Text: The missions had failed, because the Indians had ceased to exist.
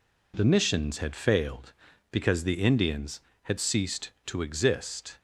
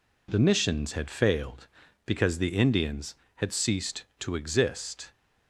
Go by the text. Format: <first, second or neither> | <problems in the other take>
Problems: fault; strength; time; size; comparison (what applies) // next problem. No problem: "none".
neither | none